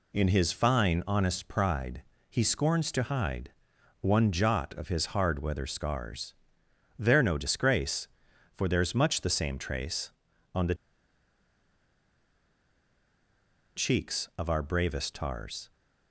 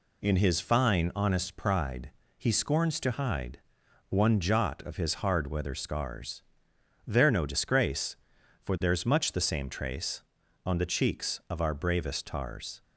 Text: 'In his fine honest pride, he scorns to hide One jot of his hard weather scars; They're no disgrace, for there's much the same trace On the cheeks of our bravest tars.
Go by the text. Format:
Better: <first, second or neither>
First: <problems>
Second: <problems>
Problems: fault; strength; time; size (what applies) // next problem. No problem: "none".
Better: second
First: pauses between "hide" and "One"; noticeable; at 3.5 s; 0.50 s long // pauses between "the" and "cheeks"; strong; at 10.7 s; 3.0 s long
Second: pauses between "hide" and "One"; noticeable; at 3.5 s; 0.50 s long